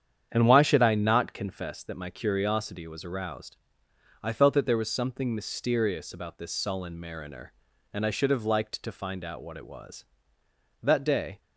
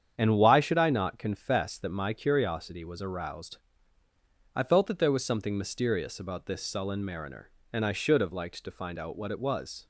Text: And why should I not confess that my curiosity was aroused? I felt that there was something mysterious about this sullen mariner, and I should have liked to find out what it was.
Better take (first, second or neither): second